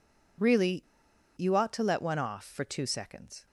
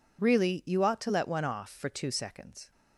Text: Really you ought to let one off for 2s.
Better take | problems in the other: second | pauses between "Really" and "you"; noticeable; at 0.8 s; 0.54 s long

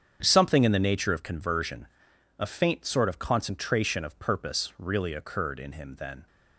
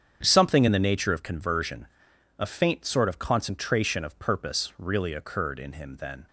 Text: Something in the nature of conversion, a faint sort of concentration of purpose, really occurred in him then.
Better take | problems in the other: neither | starts louder than the rest; strong; the same in both

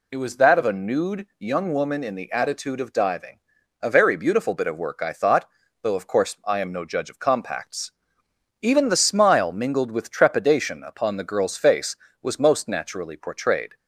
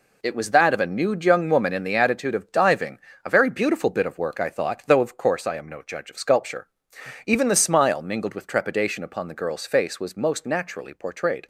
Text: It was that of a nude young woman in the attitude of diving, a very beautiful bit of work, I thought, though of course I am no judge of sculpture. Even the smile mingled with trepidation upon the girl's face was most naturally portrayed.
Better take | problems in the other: second | says "compacts" for "sculpture"; at 7.1 s

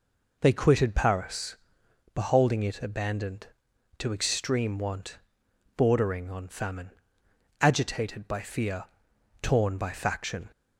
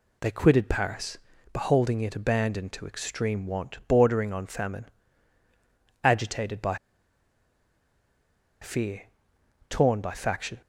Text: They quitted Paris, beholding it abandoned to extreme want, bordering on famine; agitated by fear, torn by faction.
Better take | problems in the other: first | pauses between "by" and "fear"; strong; at 6.7 s; 1.8 s long

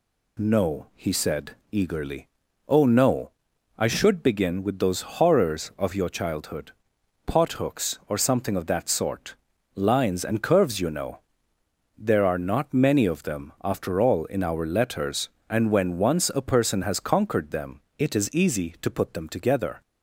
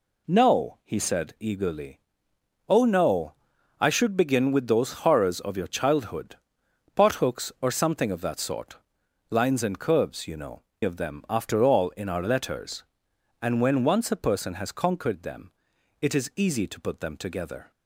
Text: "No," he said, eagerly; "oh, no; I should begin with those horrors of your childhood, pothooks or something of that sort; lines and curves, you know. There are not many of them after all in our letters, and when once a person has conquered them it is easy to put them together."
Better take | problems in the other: first | skips "There are not many"; at 10.7 s // pauses between "them" and "it"; noticeable; at 15.5 s; 0.48 s long; slight in the first

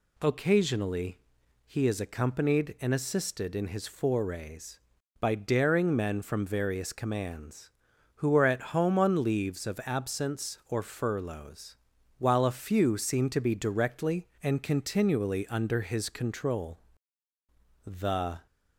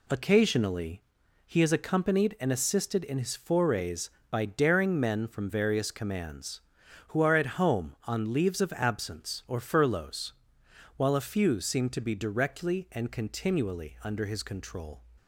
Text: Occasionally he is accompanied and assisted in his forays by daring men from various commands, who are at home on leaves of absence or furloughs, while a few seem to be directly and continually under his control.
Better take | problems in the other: second | pauses between "Occasionally" and "he"; noticeable; at 1.1 s; 0.46 s long; also in the second // goes on to say "The"; noticeable; from 17.8 s on; 0.62 s long

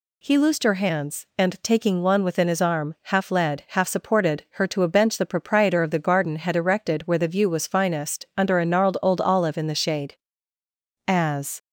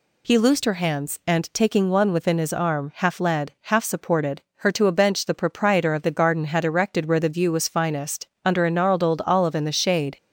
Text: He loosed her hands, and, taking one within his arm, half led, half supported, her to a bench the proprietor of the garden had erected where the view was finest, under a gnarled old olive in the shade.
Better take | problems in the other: second | goes on to say "As"; from 11.0 s on; 0.54 s long

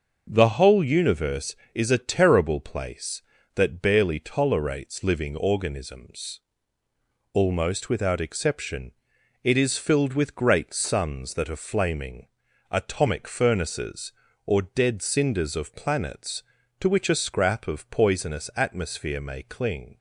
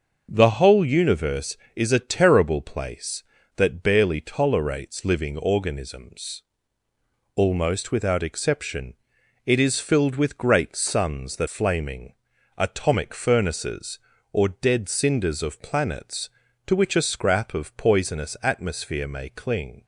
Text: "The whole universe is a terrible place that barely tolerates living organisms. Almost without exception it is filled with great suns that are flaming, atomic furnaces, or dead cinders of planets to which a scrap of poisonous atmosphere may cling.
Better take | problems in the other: first | starts louder than the rest; noticeable; until 1.3 s; 6 dB; noticeable in the first // pauses between "exception" and "it"; noticeable; at 8.9 s; 0.50 s long; noticeable in the first // skips "are"; at 11.4 s

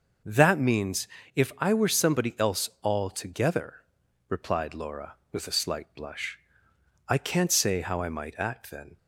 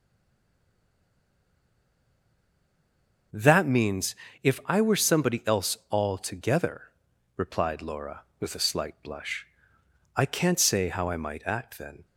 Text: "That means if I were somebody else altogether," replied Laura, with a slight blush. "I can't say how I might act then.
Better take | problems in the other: first | stays silent before the first word; strong; until 3.3 s; 3.3 s long // pauses between "means" and "if"; slight; at 4.1 s; 0.28 s long; slight in the first

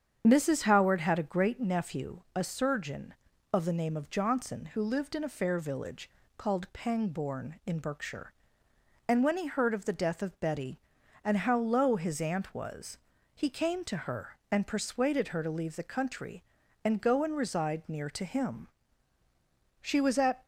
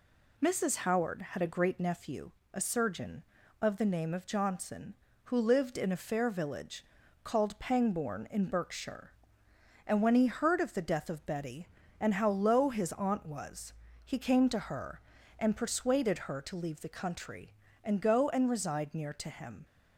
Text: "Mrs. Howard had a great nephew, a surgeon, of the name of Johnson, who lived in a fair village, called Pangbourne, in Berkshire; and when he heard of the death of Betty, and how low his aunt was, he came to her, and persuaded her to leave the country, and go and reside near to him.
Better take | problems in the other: second | starts louder than the rest; strong; until 1.2 s; 8 dB // goes on to say "She was at"; noticeable; from 19.7 s on; 0.64 s long

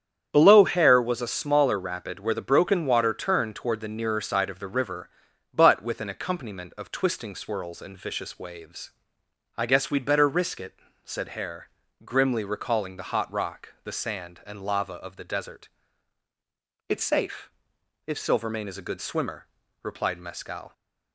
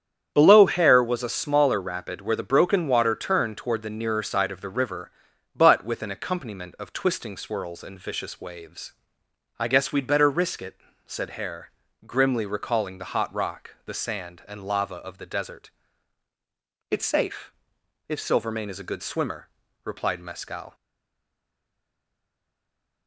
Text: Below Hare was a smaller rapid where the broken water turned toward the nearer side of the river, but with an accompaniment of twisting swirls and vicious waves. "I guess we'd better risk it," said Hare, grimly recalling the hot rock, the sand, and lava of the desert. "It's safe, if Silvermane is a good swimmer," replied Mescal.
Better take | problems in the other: first | starts louder than the rest; strong; until 1.3 s; 8.5 dB; strong in the first // stays silent after the last word; from 20.7 s on; 2.3 s long

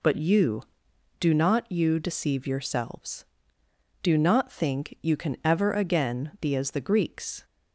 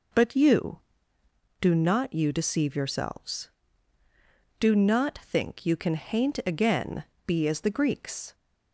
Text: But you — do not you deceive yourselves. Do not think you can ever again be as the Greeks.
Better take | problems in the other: first | says "haint" for "ever"; at 5.9 s // pauses between "again" and "be"; slight; at 7.0 s; 0.22 s long

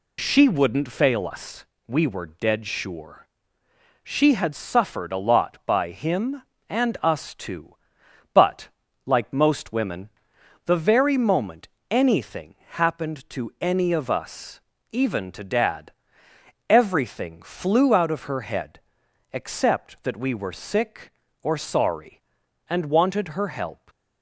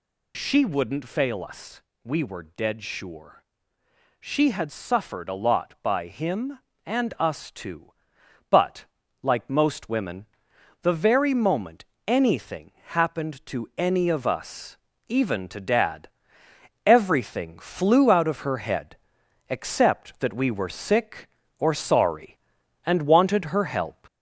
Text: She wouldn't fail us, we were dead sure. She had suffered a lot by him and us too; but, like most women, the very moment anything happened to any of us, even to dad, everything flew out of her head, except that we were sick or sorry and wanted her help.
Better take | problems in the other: first | gets louder; slight; throughout; 3 dB // pauses between "moment" and "anything"; slight; at 11.8 s; 0.20 s long; slight in the first // pauses between "anything" and "happened"; slight; at 12.7 s; 0.16 s long; slight in the first

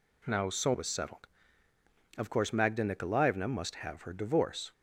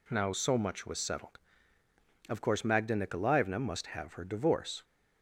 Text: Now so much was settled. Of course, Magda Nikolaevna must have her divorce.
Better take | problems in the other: second | skips "much"; at 0.7 s

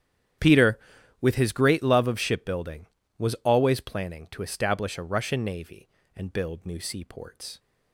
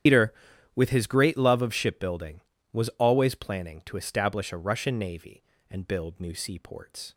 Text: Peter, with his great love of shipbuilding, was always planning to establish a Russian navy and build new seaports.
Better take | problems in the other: first | loses the start of "Peter"; at 0.0 s; 115 ms // starts louder than the rest; strong; until 1.4 s; 9.5 dB; strong in the first

